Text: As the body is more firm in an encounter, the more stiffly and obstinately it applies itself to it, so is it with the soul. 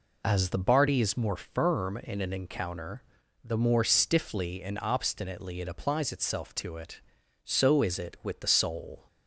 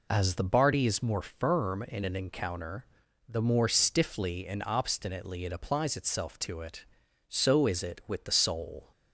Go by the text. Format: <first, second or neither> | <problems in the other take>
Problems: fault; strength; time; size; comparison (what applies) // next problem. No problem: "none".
neither | none